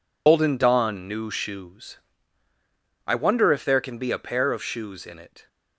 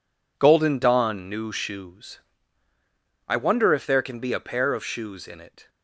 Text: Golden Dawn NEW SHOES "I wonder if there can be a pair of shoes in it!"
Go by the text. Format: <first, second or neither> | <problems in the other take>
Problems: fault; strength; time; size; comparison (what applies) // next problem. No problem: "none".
second | loses the start of "Golden"; at 0.2 s; 105 ms // pauses between "SHOES" and "I"; at 1.9 s; 1.0 s long; also in the second